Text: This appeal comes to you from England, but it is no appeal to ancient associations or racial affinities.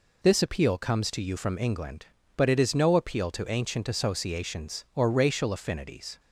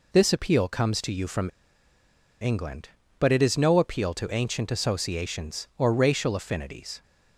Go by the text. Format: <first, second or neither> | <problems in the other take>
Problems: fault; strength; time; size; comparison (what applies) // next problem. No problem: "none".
first | pauses between "from" and "England"; noticeable; at 1.4 s; 0.91 s long